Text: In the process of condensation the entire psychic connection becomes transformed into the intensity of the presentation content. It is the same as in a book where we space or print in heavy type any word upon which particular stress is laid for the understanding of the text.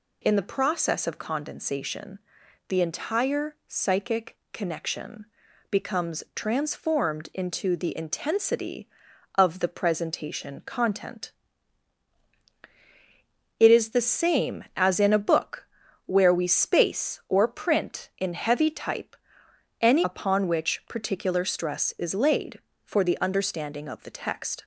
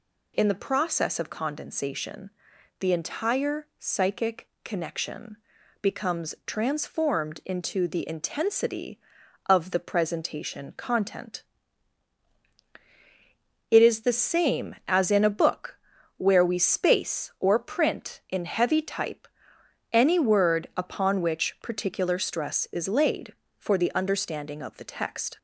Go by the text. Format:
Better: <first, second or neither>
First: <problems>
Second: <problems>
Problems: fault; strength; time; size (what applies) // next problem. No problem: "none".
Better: second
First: pauses between "condensation" and "the"; noticeable; at 2.2 s; 0.48 s long // pauses between "psychic" and "connection"; slight; at 4.3 s; 0.16 s long // pauses between "connection" and "becomes"; at 5.2 s; 0.44 s long // pauses between "book" and "where"; at 15.6 s; 0.40 s long // pauses between "type" and "any"; noticeable; at 19.1 s; 0.64 s long // skips "word"; at 20.0 s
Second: pauses between "condensation" and "the"; noticeable; at 2.3 s; 0.48 s long // pauses between "psychic" and "connection"; slight; at 4.4 s; 0.16 s long // pauses between "connection" and "becomes"; at 5.3 s; 0.44 s long // pauses between "book" and "where"; at 15.7 s; 0.40 s long // pauses between "type" and "any"; noticeable; at 19.2 s; 0.64 s long